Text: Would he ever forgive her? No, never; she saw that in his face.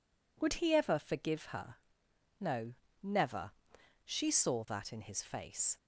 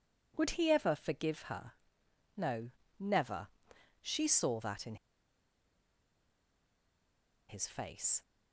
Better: first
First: none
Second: pauses between "in" and "his"; strong; at 4.9 s; 2.5 s long

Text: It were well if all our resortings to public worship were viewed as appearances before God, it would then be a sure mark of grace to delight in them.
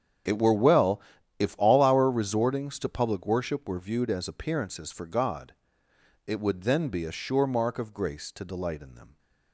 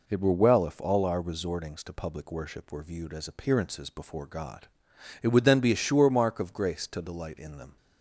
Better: second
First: starts louder than the rest; strong; until 1.6 s; 8.5 dB // pauses between "well" and "if"; at 1.0 s; 0.38 s long // says "for" for "before"; at 4.9 s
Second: none

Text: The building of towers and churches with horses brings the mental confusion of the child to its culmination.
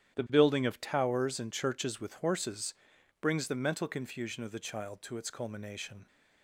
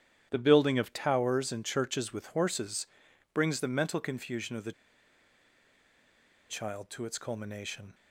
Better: first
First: starts louder than the rest; strong; until 1.2 s; 11.5 dB // pauses between "horses" and "brings"; noticeable; at 2.7 s; 0.48 s long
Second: starts louder than the rest; strong; until 1.3 s; 10 dB // pauses between "horses" and "brings"; noticeable; at 2.8 s; 0.48 s long // pauses between "the" and "child"; strong; at 4.7 s; 1.7 s long

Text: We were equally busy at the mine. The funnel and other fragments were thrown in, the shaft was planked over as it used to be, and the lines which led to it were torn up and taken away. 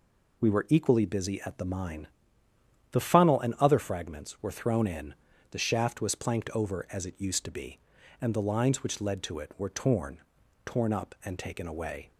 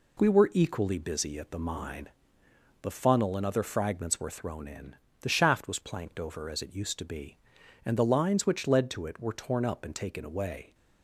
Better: second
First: says "torn" twice; at 10.6 s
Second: none

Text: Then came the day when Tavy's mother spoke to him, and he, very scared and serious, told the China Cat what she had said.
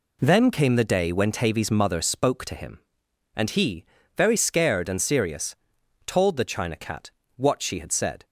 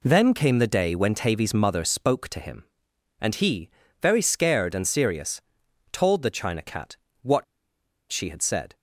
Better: first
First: pauses between "Cat" and "what"; slight; at 7.1 s; 0.24 s long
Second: pauses between "Cat" and "what"; slight; at 6.9 s; 0.24 s long // pauses between "what" and "she"; noticeable; at 7.4 s; 0.66 s long

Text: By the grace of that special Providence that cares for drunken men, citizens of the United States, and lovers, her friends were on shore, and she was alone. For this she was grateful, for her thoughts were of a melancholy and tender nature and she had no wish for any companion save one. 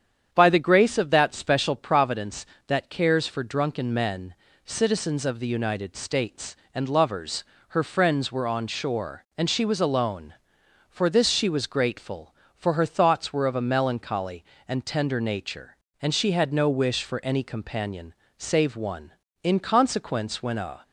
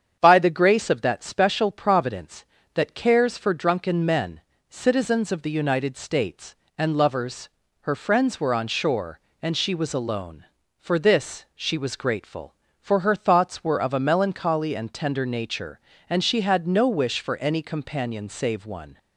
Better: second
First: starts louder than the rest; strong; until 1.3 s; 8.5 dB // pauses between "companion" and "save"; slight; at 18.1 s; 0.24 s long // goes on to say "In consequence when a"; from 19.4 s on; 1.4 s long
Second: starts louder than the rest; strong; until 1.2 s; 8 dB

